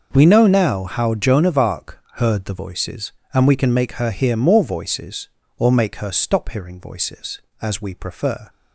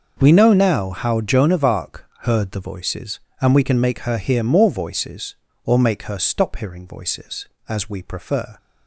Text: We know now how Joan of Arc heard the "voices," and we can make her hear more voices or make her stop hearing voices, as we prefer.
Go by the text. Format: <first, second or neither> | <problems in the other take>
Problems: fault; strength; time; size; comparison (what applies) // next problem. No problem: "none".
neither | pauses between "Arc" and "heard"; slight; the same in both